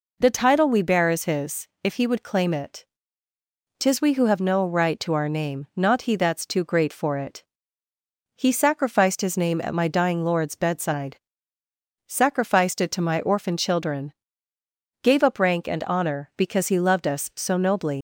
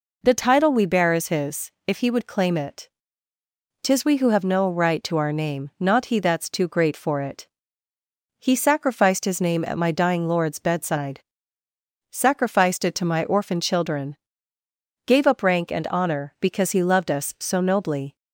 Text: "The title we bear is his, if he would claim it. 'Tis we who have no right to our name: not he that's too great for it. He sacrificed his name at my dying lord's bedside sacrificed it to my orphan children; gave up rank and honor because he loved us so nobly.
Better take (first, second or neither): second